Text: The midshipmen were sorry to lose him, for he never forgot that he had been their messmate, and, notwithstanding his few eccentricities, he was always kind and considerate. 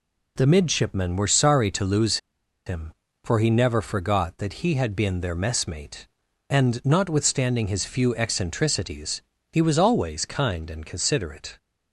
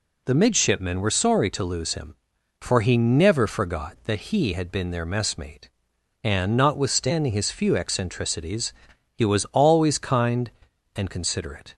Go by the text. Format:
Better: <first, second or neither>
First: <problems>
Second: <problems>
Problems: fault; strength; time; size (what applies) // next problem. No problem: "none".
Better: second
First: pauses between "lose" and "him"; noticeable; at 2.1 s; 0.49 s long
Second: none